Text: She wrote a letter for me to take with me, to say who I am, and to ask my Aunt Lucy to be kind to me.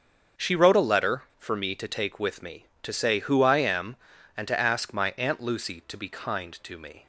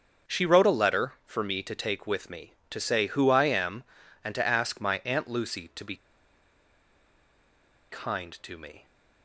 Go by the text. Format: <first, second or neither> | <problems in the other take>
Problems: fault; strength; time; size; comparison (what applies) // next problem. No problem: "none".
first | starts louder than the rest; until 1.3 s; 6.5 dB; also in the first // pauses between "be" and "kind"; strong; at 5.9 s; 1.9 s long